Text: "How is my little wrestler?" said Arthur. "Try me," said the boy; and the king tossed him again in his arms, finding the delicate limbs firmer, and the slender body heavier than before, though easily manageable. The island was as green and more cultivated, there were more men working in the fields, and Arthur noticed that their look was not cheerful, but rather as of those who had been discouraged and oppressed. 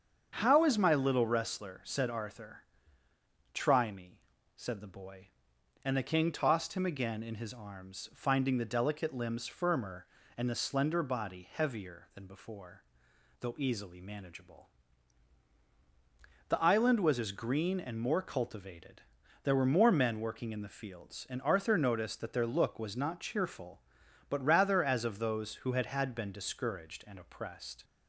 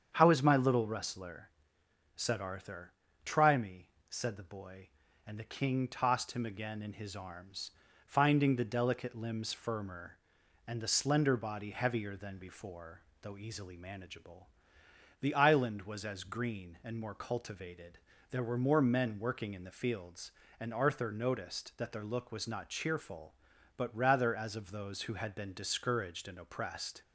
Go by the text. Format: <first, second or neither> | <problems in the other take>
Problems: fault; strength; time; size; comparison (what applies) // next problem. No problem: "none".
second | starts louder than the rest; strong; until 1.3 s; 7.5 dB; strong in the second // says "had" twice; at 25.8 s